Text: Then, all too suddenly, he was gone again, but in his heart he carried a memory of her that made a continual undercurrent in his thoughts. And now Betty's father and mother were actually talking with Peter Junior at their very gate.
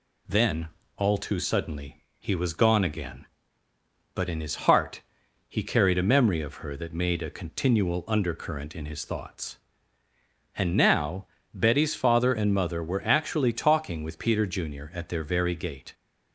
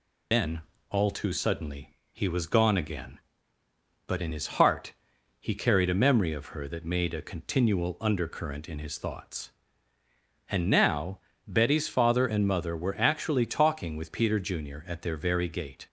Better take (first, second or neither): first